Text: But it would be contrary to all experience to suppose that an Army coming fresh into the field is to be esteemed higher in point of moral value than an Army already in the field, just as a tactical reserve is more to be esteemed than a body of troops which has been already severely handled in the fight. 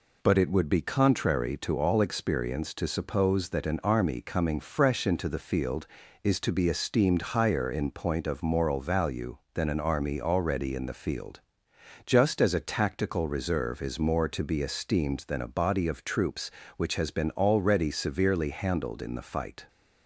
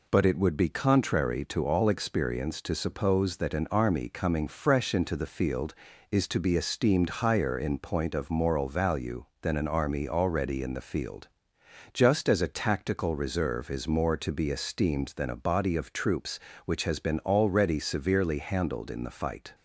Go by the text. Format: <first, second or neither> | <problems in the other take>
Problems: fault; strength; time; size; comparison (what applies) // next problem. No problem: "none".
neither | none